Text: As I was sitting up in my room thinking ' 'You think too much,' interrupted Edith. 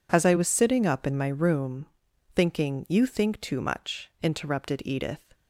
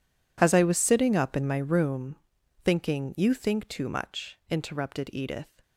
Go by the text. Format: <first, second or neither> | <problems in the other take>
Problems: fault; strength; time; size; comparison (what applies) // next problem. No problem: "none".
first | gets quieter; strong; throughout; 19 dB // pauses between "room" and "thinking"; noticeable; at 2.1 s; 0.48 s long; noticeable in the first